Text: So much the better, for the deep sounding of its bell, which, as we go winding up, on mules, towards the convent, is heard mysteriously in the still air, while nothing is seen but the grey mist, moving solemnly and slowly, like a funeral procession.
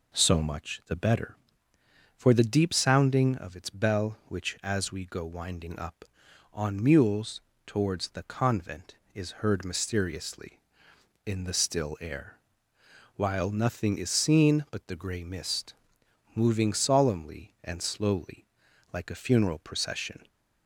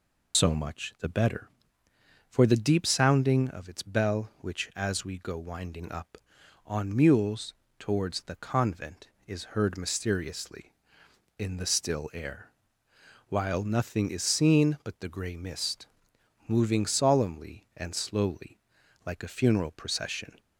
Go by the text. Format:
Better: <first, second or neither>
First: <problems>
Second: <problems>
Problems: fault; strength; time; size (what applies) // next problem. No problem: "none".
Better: first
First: none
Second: loses the start of "So"; at 0.3 s; 85 ms